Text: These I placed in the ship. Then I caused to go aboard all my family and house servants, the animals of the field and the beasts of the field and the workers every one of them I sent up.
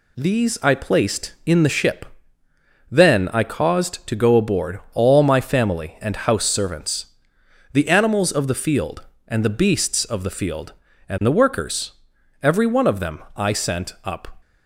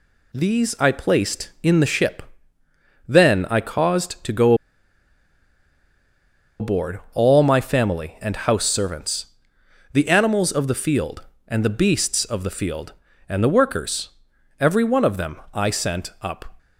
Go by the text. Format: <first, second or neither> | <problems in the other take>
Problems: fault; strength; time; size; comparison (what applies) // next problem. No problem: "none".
first | pauses between "go" and "aboard"; strong; at 4.5 s; 2.0 s long // pauses between "workers" and "every"; noticeable; at 14.0 s; 0.50 s long; noticeable in the first